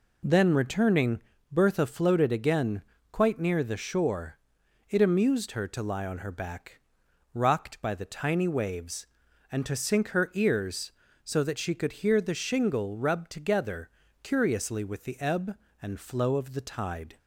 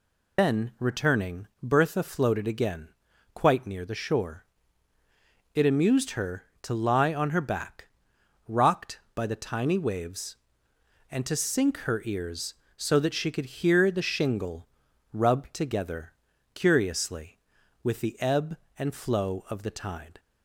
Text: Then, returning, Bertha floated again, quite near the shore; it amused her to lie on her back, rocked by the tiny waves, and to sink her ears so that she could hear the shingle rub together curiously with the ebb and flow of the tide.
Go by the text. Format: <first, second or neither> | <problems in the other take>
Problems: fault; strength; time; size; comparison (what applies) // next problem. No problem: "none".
first | loses the start of "Then"; at 0.3 s; 155 ms // pauses between "shingle" and "rub"; at 14.6 s; 0.44 s long // pauses between "together" and "curiously"; at 16.1 s; 0.40 s long; slight in the first